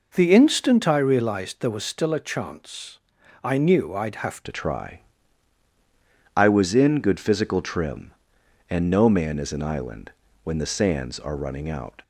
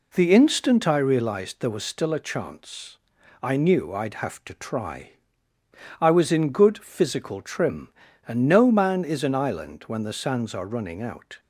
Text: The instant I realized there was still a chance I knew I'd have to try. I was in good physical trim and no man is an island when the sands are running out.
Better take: second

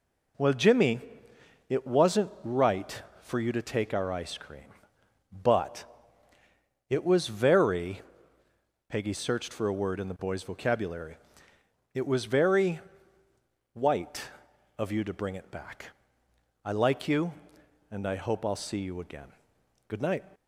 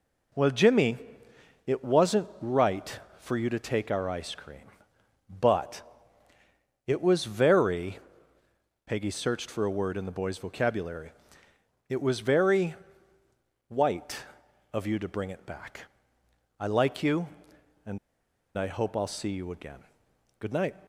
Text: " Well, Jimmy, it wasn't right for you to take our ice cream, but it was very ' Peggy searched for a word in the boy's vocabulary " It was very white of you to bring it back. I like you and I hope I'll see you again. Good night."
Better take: first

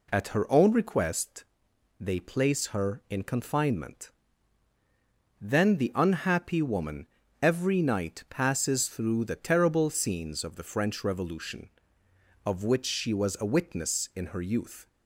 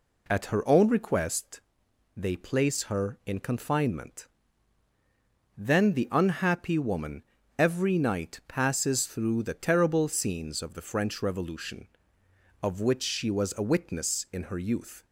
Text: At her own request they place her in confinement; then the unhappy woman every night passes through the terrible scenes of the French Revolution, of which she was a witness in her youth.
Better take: neither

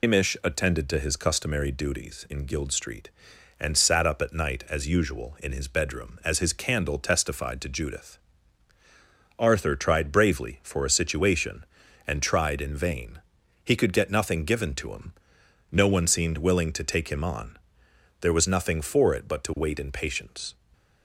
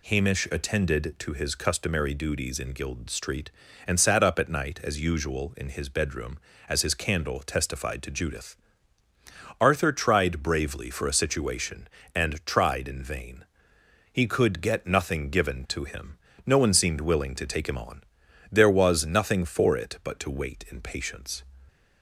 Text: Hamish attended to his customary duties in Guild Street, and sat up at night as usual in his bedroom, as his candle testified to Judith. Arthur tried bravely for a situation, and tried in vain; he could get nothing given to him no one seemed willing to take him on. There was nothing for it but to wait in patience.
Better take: second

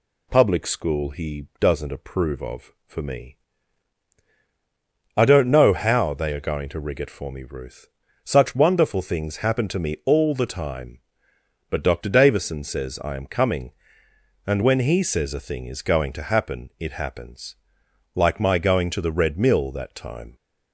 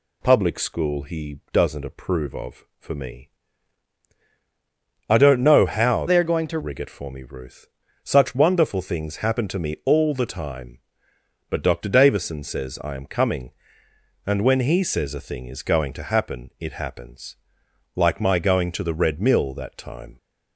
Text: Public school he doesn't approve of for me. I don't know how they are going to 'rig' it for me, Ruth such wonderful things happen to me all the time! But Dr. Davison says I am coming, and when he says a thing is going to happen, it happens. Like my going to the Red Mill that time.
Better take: first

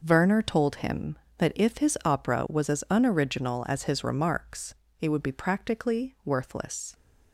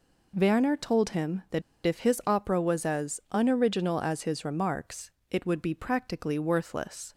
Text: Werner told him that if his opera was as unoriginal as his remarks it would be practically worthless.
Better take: first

